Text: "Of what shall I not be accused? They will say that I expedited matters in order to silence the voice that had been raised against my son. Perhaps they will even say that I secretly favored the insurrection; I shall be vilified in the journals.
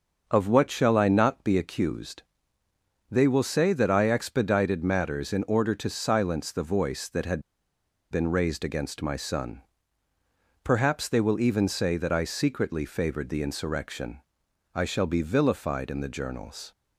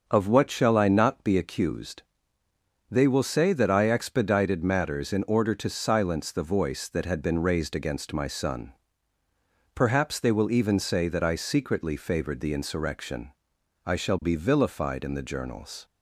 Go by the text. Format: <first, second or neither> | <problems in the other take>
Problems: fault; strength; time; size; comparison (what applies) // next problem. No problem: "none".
second | starts louder than the rest; until 1.3 s; 6 dB; also in the second // pauses between "had" and "been"; noticeable; at 7.4 s; 0.70 s long